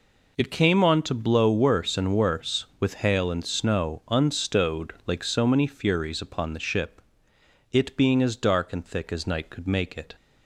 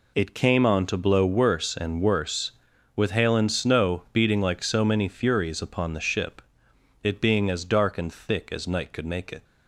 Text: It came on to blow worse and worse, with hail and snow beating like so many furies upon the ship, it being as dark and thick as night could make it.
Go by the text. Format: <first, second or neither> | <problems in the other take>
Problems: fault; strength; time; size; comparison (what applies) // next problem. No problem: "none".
second | says "unstowed" for "beating"; at 4.0 s